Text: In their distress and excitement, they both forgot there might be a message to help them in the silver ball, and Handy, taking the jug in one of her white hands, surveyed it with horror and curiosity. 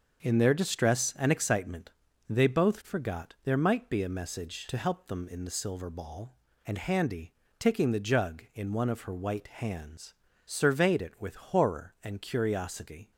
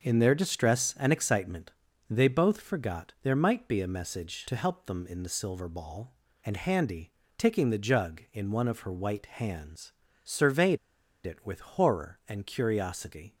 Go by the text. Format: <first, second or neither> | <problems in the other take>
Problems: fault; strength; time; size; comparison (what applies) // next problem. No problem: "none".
first | starts louder than the rest; until 1.0 s; 6 dB; also in the first // pauses between "surveyed" and "it"; noticeable; at 10.7 s; 0.48 s long